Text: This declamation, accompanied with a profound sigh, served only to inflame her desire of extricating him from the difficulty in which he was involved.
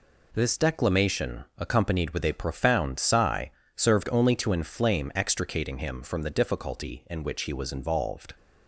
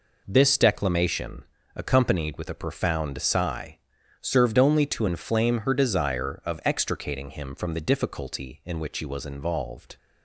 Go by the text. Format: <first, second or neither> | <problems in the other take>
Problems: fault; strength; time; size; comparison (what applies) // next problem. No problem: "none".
second | skips "her desire of"; at 5.1 s